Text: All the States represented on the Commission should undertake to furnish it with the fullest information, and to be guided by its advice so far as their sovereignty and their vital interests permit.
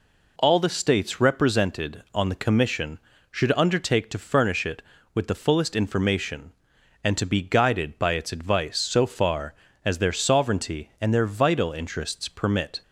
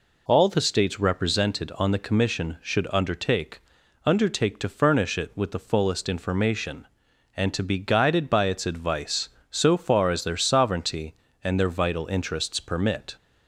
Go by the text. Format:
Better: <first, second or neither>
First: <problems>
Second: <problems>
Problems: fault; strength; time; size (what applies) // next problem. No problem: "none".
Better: first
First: none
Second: says "undertake" twice; at 4.0 s